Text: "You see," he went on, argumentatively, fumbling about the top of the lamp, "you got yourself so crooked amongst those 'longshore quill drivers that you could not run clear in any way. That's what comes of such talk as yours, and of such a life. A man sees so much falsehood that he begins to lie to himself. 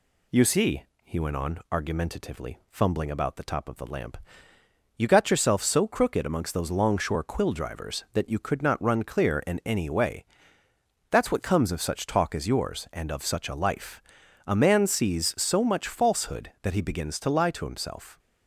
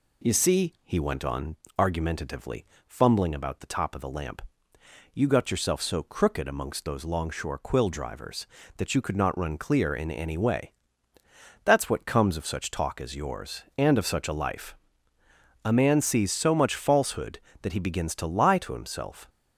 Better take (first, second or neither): neither